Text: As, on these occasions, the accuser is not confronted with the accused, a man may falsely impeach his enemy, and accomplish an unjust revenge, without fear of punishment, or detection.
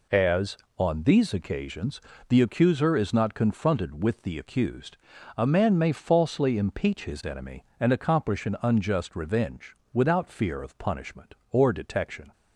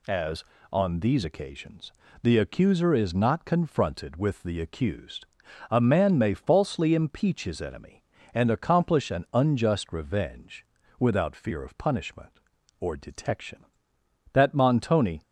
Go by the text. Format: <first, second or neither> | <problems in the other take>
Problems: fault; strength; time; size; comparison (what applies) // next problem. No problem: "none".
first | goes on to say "That Montoni"; noticeable; from 14.3 s on; 0.88 s long